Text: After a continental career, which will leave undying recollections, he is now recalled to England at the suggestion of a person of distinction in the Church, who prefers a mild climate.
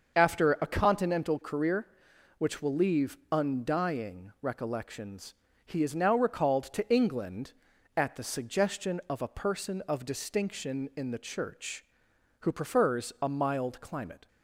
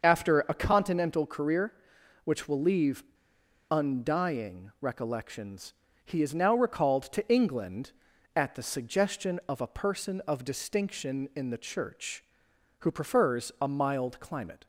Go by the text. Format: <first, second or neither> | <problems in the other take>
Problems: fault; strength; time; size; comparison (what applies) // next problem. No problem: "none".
first | starts louder than the rest; until 1.1 s; 6.5 dB; also in the first // pauses between "leave" and "undying"; noticeable; at 3.0 s; 0.67 s long